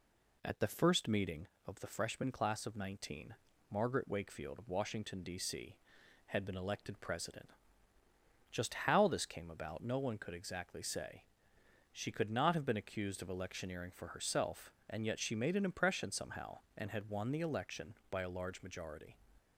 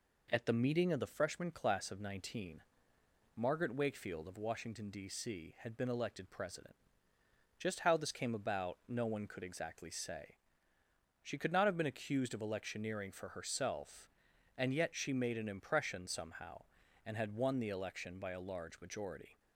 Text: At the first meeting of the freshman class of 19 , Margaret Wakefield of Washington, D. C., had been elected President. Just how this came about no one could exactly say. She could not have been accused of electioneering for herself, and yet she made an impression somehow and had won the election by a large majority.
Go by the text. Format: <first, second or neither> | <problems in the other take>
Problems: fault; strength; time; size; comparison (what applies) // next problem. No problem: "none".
first | skips "first"; at 0.5 s